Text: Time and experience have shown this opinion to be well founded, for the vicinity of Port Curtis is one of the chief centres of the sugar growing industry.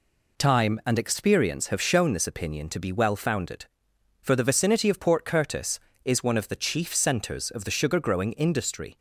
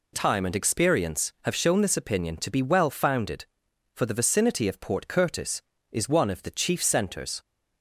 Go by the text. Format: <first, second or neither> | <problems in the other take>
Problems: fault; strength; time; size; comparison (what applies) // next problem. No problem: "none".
first | stops before "of the sugar growing industry"; at 7.4 s